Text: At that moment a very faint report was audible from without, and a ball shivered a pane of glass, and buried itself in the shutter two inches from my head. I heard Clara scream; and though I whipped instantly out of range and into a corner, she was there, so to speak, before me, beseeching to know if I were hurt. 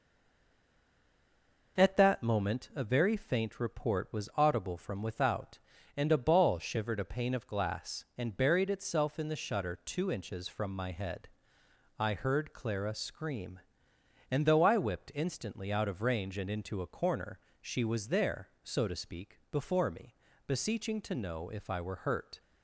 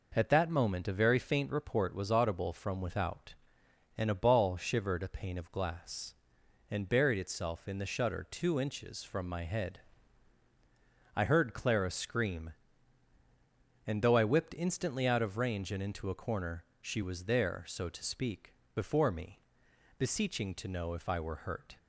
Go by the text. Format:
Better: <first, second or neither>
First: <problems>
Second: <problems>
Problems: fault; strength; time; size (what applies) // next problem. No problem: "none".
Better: second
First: stays silent before the first word; noticeable; until 1.7 s; 1.7 s long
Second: none